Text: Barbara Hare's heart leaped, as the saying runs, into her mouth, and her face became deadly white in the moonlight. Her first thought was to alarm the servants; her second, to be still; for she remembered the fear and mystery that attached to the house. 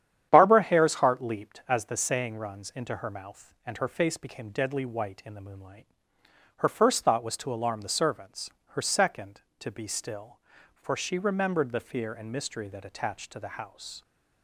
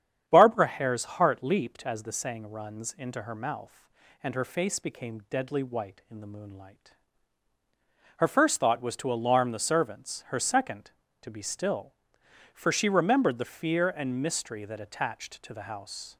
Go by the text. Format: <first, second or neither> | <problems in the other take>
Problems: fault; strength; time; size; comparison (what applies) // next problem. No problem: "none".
neither | starts louder than the rest; strong; the same in both